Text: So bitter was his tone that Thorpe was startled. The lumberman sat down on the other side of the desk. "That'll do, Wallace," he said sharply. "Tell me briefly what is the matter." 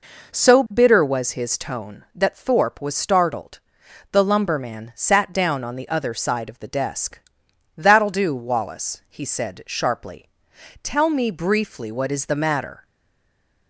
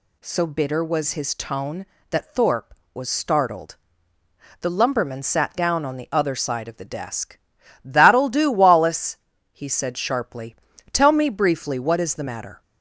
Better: second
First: stays silent after the last word; slight; from 12.8 s on; 0.8 s long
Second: none

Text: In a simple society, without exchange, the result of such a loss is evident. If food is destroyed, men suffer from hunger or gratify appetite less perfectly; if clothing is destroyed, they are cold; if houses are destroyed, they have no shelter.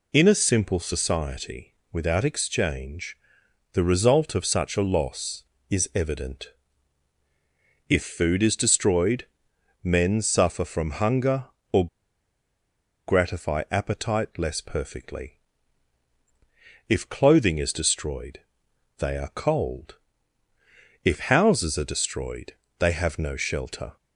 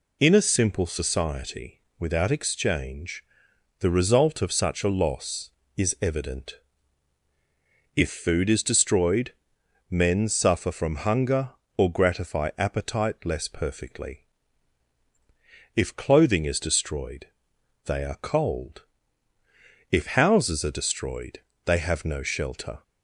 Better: second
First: pauses between "or" and "gratify"; at 11.8 s; 1.2 s long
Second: none

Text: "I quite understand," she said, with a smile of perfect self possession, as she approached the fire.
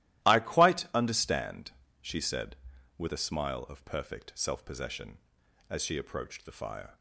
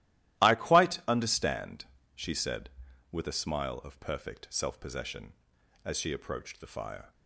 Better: neither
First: starts louder than the rest; strong; until 1.3 s; 14.5 dB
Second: starts louder than the rest; strong; until 1.4 s; 14.5 dB

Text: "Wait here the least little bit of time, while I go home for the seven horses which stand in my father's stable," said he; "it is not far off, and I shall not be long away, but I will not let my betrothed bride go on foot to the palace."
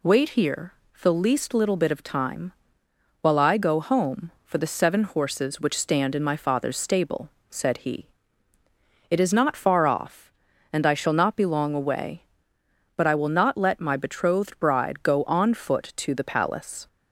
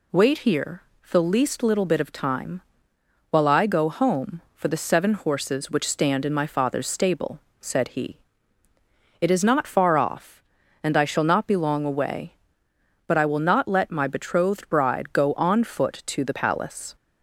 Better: neither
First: pauses between "here" and "the"; slight; at 0.7 s; 0.30 s long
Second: pauses between "here" and "the"; slight; at 0.8 s; 0.30 s long

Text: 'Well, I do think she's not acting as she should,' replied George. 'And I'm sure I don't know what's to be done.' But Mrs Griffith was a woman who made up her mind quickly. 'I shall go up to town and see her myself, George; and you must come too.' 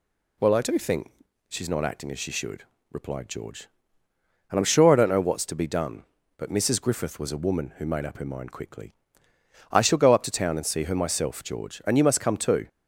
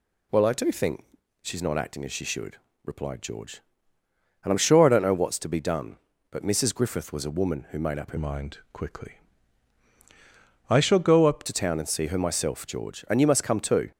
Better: first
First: pauses between "think" and "she's"; at 1.1 s; 0.38 s long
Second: pauses between "think" and "she's"; at 1.0 s; 0.38 s long // changes voice from "mind" to "up"; from 8.1 to 11.4 s; 3.3 s long

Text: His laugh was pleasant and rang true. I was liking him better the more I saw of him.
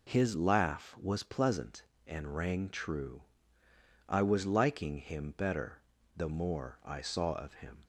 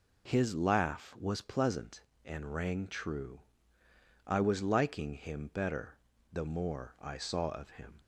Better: neither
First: pauses between "better" and "the"; slight; at 5.8 s; 0.34 s long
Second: pauses between "better" and "the"; slight; at 5.9 s; 0.34 s long

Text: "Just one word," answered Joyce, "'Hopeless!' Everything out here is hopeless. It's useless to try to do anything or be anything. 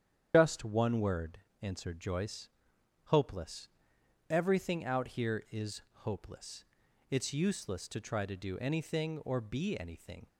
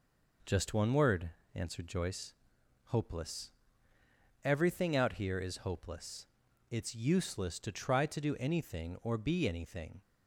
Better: second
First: loses the start of "Just"; at 0.3 s; 125 ms // starts louder than the rest; strong; until 1.3 s; 9 dB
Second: none

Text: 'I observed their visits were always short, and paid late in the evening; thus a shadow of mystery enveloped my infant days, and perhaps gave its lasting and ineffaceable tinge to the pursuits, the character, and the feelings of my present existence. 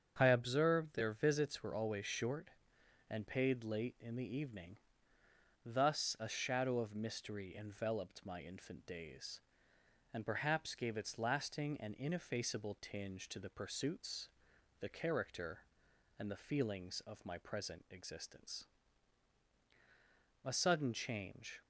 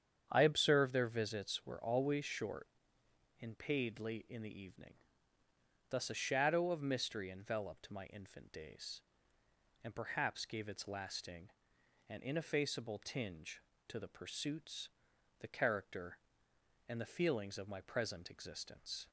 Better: second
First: starts louder than the rest; strong; until 1.1 s; 8 dB // goes on to say "A sudden change"; noticeable; from 20.4 s on; 1.1 s long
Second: starts louder than the rest; strong; until 1.3 s; 8.5 dB

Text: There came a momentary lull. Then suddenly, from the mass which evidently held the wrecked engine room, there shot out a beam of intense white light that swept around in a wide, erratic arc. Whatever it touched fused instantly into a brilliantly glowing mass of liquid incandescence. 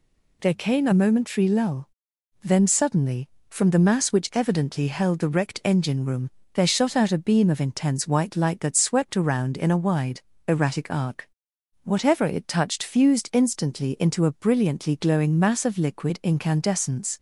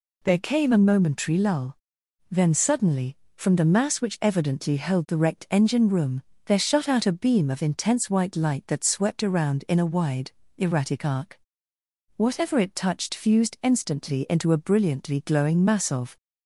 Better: first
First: none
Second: stops before "liquid incandescence"; at 16.1 s

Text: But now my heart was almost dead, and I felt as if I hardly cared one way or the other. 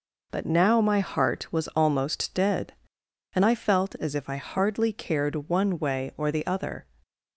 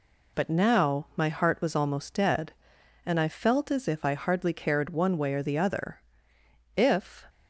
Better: first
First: none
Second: goes on to say "If"; from 6.7 s on; 0.50 s long

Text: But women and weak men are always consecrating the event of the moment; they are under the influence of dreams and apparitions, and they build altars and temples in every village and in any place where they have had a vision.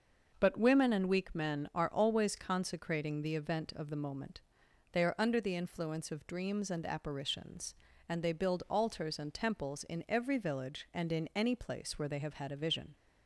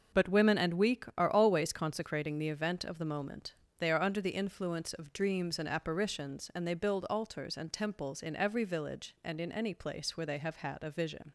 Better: first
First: starts louder than the rest; until 1.4 s; 6 dB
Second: starts louder than the rest; until 1.2 s; 6.5 dB // skips "men"; at 1.1 s

